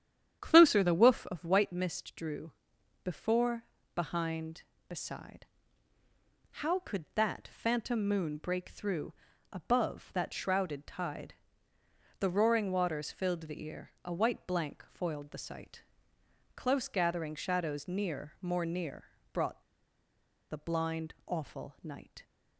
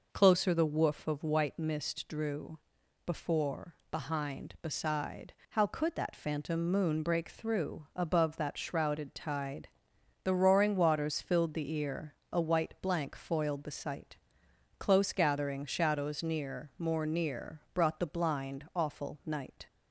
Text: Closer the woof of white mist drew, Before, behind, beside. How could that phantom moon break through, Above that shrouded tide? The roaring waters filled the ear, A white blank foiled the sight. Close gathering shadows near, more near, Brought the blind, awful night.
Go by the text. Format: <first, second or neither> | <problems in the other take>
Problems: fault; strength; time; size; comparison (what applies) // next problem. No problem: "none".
second | starts louder than the rest; strong; until 1.4 s; 9.5 dB // pauses between "Brought" and "the"; noticeable; at 19.6 s; 0.89 s long